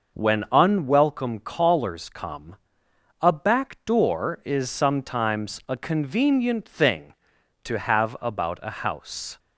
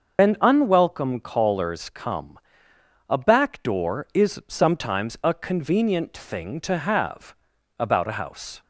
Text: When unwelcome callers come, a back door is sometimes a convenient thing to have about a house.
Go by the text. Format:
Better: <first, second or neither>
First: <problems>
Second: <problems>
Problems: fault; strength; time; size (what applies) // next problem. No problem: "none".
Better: first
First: none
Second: loses the start of "When"; at 0.1 s; 100 ms // starts louder than the rest; until 1.2 s; 6.5 dB // pauses between "have" and "about"; at 7.3 s; 0.42 s long